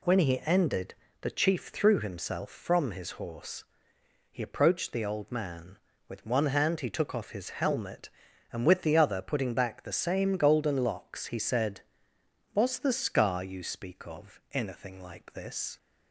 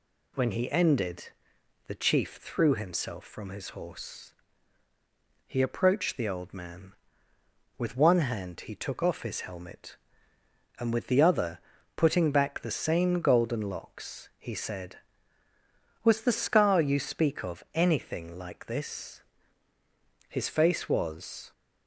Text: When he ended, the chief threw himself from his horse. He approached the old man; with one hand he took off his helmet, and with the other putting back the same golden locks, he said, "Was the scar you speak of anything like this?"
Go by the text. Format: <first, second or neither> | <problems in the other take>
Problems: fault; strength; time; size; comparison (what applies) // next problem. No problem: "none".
first | pauses between "other" and "putting"; slight; at 11.5 s; 0.36 s long // goes on to say "His face was"; noticeable; from 20.2 s on; 1.2 s long